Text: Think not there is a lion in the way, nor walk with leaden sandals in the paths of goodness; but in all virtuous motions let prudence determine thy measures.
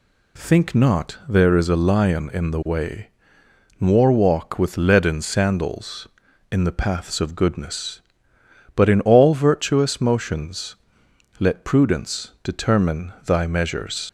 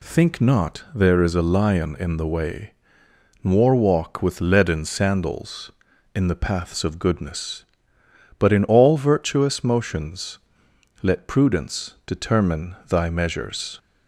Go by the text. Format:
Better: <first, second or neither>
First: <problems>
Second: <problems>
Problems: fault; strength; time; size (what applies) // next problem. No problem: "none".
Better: second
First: pauses between "motions" and "let"; noticeable; at 10.7 s; 0.64 s long // leaves "measures" unfinished; at 14.0 s; 55 ms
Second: pauses between "motions" and "let"; noticeable; at 10.3 s; 0.64 s long